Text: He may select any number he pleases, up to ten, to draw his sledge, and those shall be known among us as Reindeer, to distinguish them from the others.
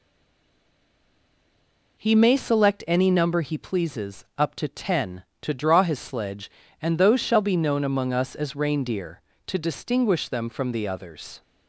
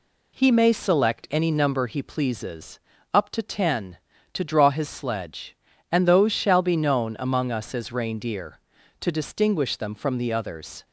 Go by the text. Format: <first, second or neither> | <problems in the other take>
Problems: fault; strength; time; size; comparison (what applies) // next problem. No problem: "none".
second | stays silent before the first word; noticeable; until 1.9 s; 1.9 s long